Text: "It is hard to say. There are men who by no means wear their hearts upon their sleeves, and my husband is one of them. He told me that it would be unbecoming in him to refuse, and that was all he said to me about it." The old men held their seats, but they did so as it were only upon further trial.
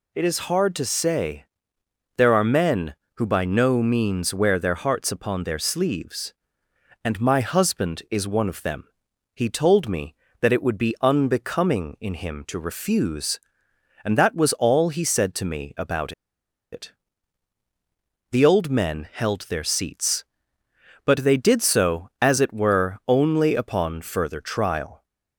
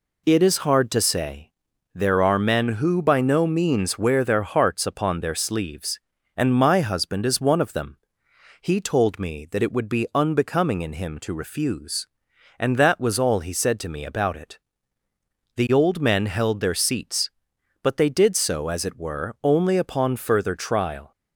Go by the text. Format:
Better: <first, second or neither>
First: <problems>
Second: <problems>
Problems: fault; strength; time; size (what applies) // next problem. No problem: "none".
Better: second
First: pauses between "about" and "it"; noticeable; at 16.1 s; 0.60 s long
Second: none